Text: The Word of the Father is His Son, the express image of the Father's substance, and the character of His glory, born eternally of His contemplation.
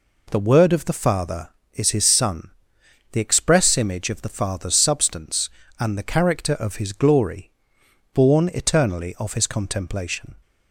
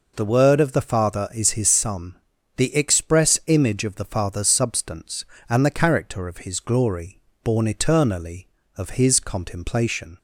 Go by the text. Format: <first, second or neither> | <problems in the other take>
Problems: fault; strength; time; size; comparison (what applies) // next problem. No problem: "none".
neither | none